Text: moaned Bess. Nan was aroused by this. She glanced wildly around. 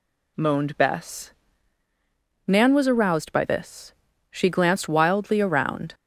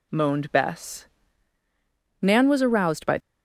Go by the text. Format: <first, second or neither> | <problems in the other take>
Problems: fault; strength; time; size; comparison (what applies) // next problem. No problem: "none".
first | stops before "this She glanced wildly around"; at 3.1 s